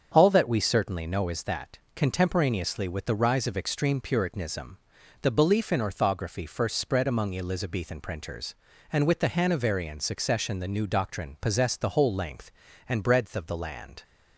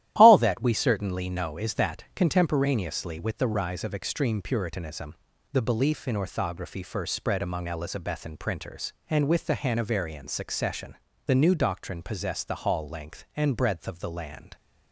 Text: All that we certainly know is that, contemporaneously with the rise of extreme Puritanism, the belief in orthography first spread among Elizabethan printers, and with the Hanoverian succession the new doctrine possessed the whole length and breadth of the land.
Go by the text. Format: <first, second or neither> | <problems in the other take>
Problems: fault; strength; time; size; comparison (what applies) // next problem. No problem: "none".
first | starts louder than the rest; strong; until 1.1 s; 13 dB; strong in the first // pauses between "succession" and "the"; slight; at 10.9 s; 0.30 s long // says "hall" for "whole"; at 12.6 s